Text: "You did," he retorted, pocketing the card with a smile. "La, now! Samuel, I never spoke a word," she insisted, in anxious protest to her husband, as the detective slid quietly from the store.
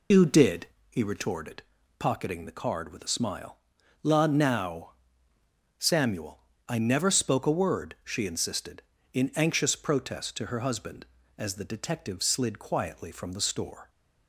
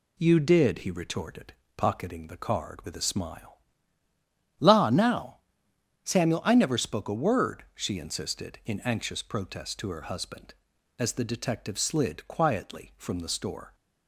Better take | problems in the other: second | loses the start of "You"; at 0.1 s; 110 ms

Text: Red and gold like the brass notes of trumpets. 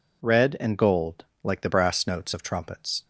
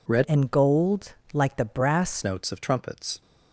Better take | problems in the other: first | changes voice from "and" to "brass"; from 0.2 to 2.2 s; 2.0 s long // pauses between "gold" and "like"; slight; at 1.1 s; 0.22 s long; slight in the first

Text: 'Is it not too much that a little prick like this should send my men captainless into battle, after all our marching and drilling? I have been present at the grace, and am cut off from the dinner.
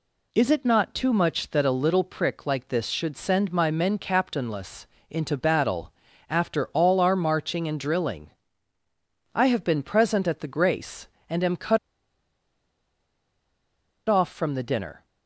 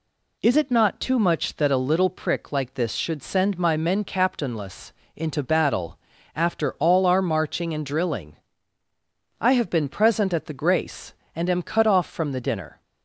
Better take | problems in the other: second | pauses between "captainless" and "into"; slight; at 4.8 s; 0.22 s long; slight in the second // pauses between "cut" and "off"; strong; at 11.7 s; 2.3 s long

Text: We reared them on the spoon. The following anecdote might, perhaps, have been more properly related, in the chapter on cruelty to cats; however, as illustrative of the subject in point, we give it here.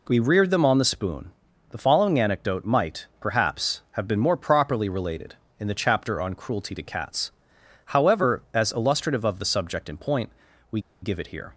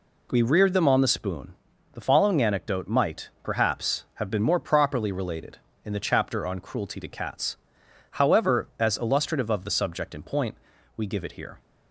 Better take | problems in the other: second | pauses between "we" and "give"; slight; at 10.7 s; 0.22 s long

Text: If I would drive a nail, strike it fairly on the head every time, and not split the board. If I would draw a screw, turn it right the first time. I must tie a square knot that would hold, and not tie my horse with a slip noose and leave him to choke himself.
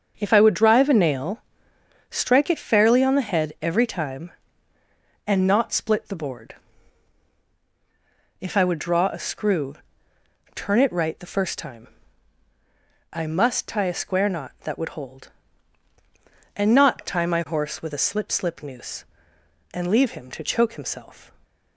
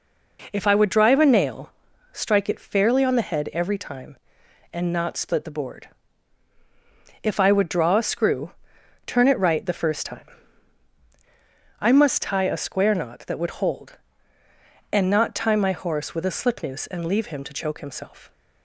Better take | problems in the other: second | starts louder than the rest; until 1.1 s; 6.5 dB // says "slip" twice; at 18.3 s

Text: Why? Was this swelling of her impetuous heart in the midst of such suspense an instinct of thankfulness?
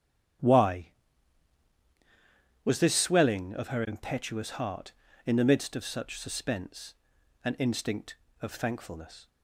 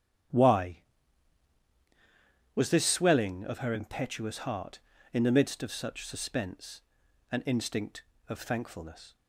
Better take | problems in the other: neither | starts louder than the rest; strong; the same in both // pauses between "suspense" and "an"; noticeable; the same in both

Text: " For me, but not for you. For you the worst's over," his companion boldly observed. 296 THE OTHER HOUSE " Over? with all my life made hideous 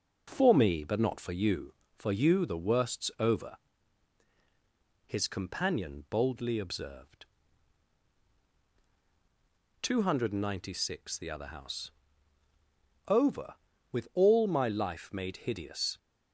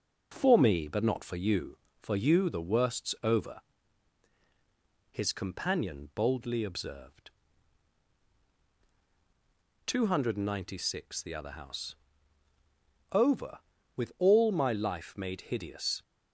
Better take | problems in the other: neither | starts louder than the rest; the same in both

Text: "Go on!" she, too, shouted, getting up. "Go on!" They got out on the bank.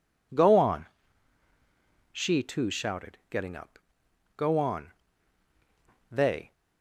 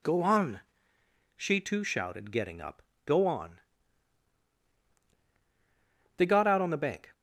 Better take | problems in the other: second | stops before "got out on the bank"; at 6.5 s

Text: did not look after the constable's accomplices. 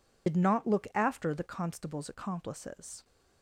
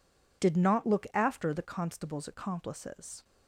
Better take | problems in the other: second | loses the start of "did"; at 0.2 s; 70 ms

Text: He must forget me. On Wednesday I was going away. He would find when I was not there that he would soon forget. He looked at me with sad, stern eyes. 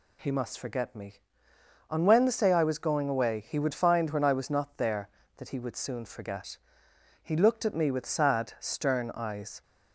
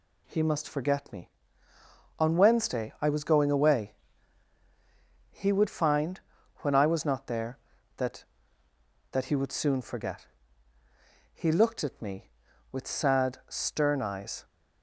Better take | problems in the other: first | pauses between "find" and "when"; at 6.2 s; 0.38 s long // says "that" twice; at 9.1 s

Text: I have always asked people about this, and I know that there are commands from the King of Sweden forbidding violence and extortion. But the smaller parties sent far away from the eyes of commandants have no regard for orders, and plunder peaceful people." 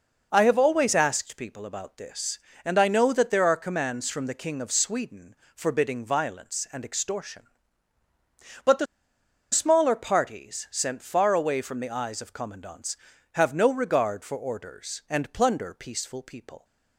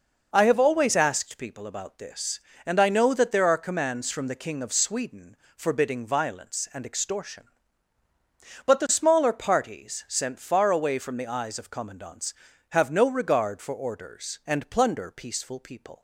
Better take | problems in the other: second | pauses between "Sweden" and "forbidding"; slight; at 5.3 s; 0.22 s long; slight in the second // pauses between "the" and "smaller"; noticeable; at 8.8 s; 0.66 s long

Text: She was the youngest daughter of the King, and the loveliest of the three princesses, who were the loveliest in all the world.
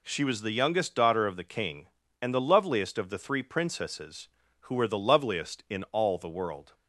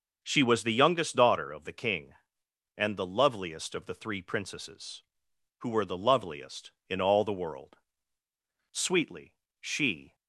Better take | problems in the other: first | starts louder than the rest; noticeable; until 1.2 s; 6 dB // goes on to say "Sweetly she"; from 8.7 s on; 1.4 s long

